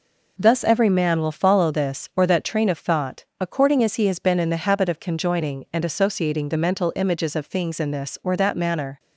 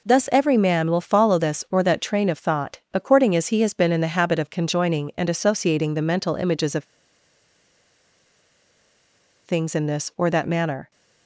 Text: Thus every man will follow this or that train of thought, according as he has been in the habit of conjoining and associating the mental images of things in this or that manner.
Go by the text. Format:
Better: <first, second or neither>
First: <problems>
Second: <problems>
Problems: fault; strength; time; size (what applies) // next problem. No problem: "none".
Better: first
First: none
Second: pauses between "of" and "things"; strong; at 6.8 s; 2.6 s long